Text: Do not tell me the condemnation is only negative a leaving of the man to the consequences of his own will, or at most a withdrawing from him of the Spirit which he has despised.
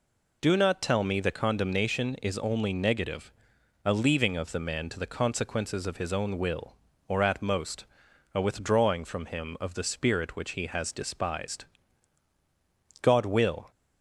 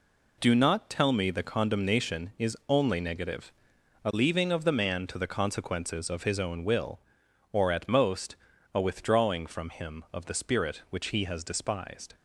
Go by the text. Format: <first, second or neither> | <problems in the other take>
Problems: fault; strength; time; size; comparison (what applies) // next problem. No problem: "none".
second | pauses between "negative" and "a"; noticeable; at 3.3 s; 0.56 s long; noticeable in the second // pauses between "most" and "a"; noticeable; at 7.8 s; 0.50 s long; also in the second // goes on to say "God will"; noticeable; from 13.0 s on; 0.68 s long